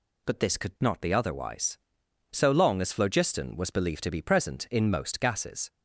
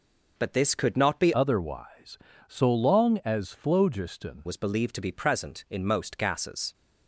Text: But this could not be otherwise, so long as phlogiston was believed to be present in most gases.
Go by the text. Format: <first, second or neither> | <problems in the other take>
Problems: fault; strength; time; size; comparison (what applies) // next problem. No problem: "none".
first | changes voice from "otherwise" to "phlogiston"; from 1.3 to 4.4 s; 3.1 s long